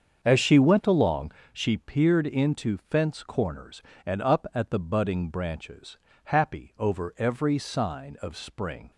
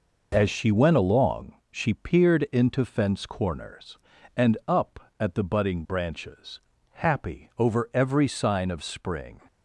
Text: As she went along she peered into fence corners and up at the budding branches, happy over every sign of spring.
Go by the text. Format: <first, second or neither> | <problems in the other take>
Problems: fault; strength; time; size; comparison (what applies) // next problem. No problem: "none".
second | starts louder than the rest; until 1.6 s; 7 dB // pauses between "along" and "she"; slight; at 1.3 s; 0.20 s long; slight in the second